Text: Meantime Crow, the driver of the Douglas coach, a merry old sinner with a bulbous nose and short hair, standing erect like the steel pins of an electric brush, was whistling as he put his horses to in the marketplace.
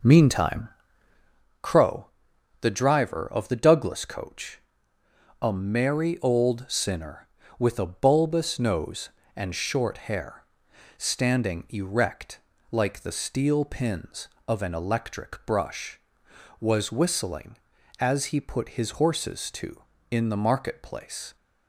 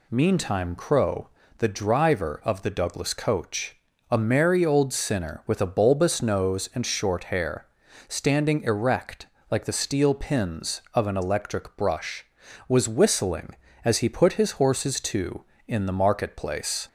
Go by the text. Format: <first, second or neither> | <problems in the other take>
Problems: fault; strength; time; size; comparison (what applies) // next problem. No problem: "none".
second | starts louder than the rest; noticeable; until 1.4 s; 5.5 dB // pauses between "Meantime" and "Crow"; noticeable; at 0.6 s; 0.94 s long // pauses between "erect" and "like"; slight; at 12.3 s; 0.32 s long; slight in the second